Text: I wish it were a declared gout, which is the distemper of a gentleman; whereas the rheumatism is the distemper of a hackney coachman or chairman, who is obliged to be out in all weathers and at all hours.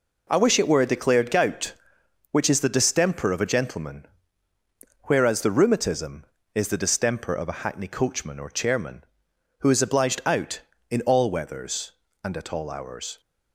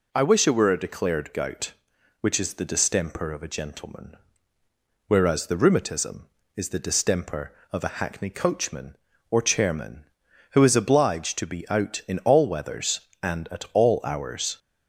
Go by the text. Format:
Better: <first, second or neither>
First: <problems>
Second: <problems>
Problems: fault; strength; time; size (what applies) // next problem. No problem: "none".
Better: second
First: skips "to be"; at 10.2 s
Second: none